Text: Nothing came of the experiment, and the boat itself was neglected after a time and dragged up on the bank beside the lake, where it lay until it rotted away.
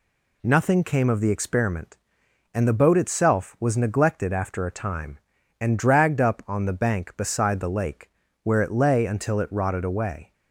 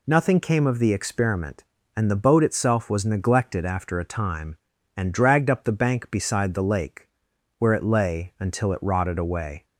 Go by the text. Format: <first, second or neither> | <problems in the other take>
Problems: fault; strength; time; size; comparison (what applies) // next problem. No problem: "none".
first | skips "on"; at 5.6 s